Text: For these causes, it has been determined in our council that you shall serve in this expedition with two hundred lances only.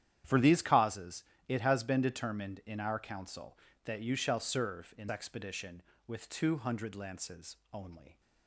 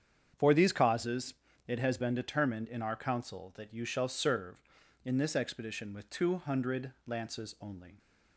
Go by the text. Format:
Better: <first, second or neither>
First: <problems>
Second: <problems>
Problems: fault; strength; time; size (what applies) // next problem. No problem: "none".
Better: second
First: starts louder than the rest; strong; until 1.5 s; 10.5 dB // skips "this"; at 5.0 s // pauses between "lances" and "only"; slight; at 7.5 s; 0.16 s long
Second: starts louder than the rest; strong; until 1.7 s; 7.5 dB